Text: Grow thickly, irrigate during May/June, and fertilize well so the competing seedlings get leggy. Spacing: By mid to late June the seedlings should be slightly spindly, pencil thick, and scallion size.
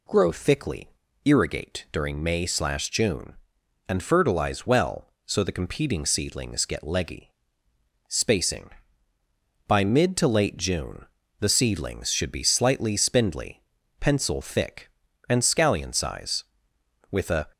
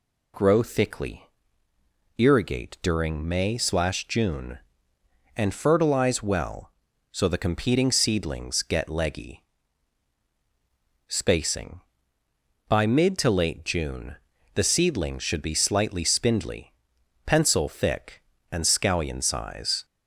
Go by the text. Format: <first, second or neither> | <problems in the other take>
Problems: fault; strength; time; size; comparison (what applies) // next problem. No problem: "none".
second | pauses between "June" and "the"; slight; at 11.0 s; 0.36 s long; also in the second // goes on to say "With a"; slight; from 17.1 s on; 0.38 s long